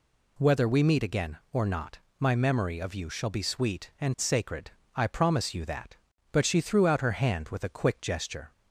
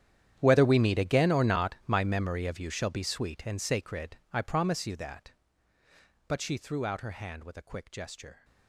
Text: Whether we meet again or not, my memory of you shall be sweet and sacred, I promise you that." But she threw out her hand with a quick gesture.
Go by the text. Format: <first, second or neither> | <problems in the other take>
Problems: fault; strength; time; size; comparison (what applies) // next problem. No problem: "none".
first | gets quieter; strong; throughout; 19 dB